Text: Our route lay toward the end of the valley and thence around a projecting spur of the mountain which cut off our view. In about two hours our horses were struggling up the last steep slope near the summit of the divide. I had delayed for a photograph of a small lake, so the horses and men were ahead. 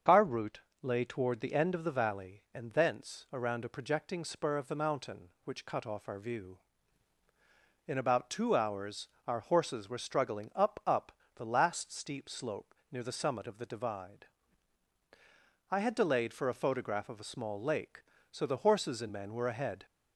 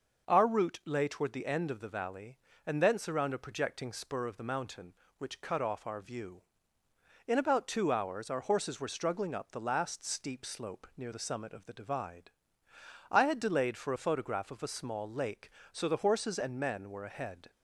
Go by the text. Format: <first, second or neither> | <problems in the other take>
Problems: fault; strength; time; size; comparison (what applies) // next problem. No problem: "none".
second | starts louder than the rest; strong; until 1.2 s; 7 dB // pauses between "route" and "lay"; slight; at 0.6 s; 0.22 s long // pauses between "hours" and "our"; slight; at 9.0 s; 0.18 s long // says "up" twice; at 10.8 s // pauses between "slope" and "near"; slight; at 12.7 s; 0.16 s long